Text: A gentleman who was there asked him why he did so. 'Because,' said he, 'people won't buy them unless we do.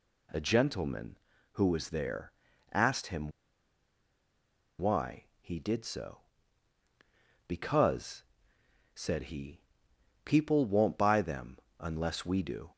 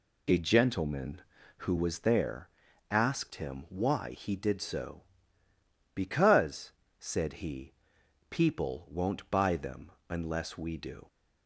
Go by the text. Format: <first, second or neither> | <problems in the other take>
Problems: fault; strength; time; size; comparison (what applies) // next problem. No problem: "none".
second | pauses between "there" and "asked"; at 2.3 s; 0.40 s long; also in the second // pauses between "him" and "why"; strong; at 3.2 s; 1.4 s long // pauses between "them" and "unless"; slight; at 11.5 s; 0.18 s long; slight in the second